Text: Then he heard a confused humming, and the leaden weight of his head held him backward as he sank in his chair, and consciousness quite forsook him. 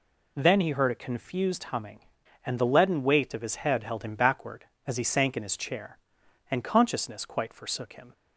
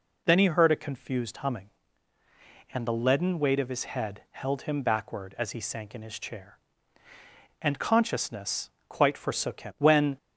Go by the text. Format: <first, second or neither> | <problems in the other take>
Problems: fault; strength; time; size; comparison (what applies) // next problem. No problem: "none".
first | pauses between "consciousness" and "quite"; slight; at 8.6 s; 0.20 s long // goes on to say "When"; slight; from 9.7 s on; 0.38 s long